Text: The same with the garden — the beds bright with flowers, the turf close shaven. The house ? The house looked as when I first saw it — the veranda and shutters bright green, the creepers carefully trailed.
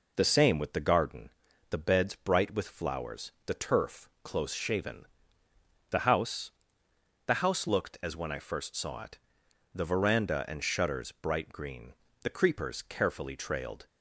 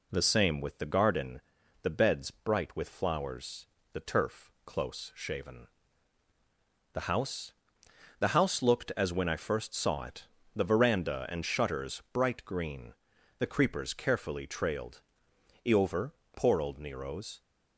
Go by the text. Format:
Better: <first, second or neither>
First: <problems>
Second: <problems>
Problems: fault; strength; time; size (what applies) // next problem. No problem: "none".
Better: first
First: none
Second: goes on to say "Eover poor old Nero's"; strong; from 15.6 s on; 1.7 s long